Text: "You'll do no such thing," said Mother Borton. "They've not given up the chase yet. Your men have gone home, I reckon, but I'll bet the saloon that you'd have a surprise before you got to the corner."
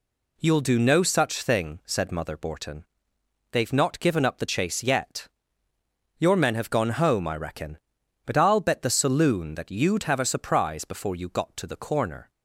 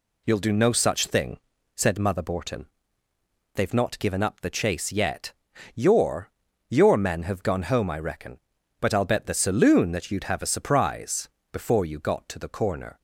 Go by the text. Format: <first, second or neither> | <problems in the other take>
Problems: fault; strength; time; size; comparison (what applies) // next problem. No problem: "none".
first | says "Your" twice; at 6.6 s // pauses between "surprise" and "before"; slight; at 11.2 s; 0.24 s long